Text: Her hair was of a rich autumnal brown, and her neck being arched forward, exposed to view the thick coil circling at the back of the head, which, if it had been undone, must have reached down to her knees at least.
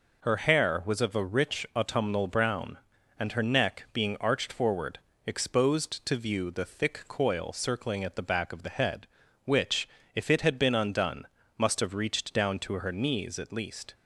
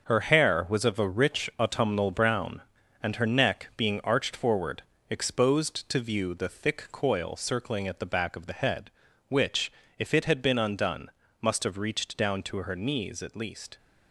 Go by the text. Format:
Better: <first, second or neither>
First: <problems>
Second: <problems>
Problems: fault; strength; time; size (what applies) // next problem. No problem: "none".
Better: first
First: none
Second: gets quieter; strong; throughout; 8 dB